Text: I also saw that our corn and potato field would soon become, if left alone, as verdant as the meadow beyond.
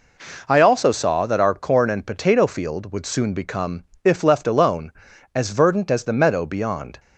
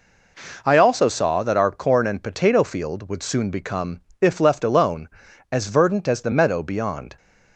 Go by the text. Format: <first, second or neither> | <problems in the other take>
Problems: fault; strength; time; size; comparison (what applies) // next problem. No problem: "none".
neither | none